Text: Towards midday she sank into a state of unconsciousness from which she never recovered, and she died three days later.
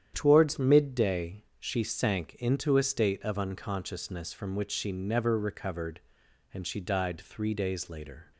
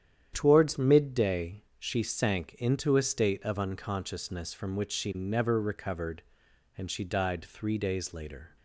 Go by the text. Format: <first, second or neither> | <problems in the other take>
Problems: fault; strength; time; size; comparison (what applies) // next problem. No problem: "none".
neither | starts louder than the rest; strong; the same in both // pauses between "midday" and "she"; slight; the same in both